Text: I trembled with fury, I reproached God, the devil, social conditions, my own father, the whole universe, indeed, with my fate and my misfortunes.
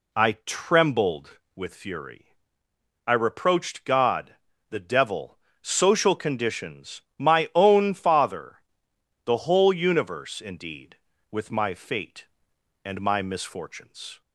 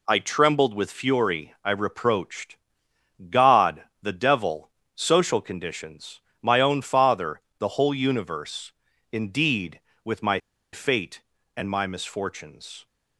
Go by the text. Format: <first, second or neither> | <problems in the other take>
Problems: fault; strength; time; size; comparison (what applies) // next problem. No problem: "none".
first | pauses between "reproached" and "God"; noticeable; at 2.5 s; 0.74 s long // pauses between "my" and "fate"; slight; at 10.3 s; 0.35 s long